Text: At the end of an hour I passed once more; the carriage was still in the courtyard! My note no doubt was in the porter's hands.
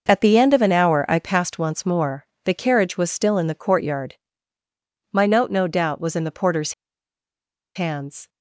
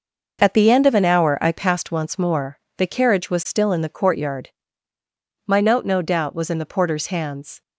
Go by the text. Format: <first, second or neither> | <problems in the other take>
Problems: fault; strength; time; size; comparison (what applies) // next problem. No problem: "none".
second | pauses between "porter's" and "hands"; at 6.7 s; 1.0 s long